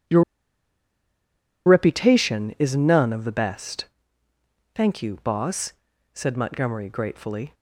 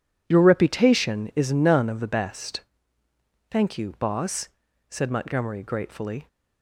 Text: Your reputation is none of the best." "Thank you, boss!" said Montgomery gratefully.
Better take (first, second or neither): second